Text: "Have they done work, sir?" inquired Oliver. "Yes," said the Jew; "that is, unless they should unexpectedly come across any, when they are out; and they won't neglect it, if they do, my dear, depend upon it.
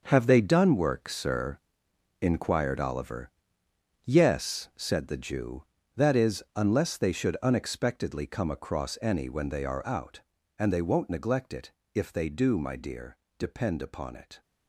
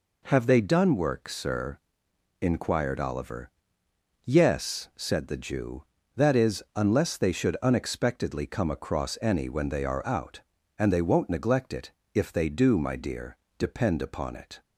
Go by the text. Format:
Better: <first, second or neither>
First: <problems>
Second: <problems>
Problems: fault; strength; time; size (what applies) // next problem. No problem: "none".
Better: second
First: gets quieter; strong; throughout; 10.5 dB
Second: none